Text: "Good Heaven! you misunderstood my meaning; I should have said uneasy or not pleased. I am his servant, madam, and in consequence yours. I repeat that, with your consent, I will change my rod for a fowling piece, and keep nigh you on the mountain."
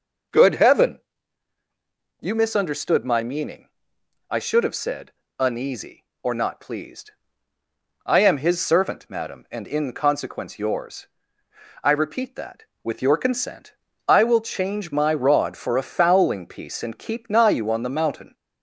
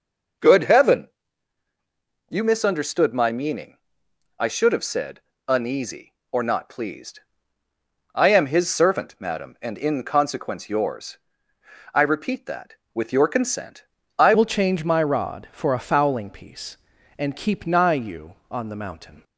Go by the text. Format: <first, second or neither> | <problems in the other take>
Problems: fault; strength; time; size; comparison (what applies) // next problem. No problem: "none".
first | pauses between "said" and "uneasy"; slight; at 5.2 s; 0.26 s long; slight in the first // changes voice at "will"; from 14.3 s on; 4.9 s long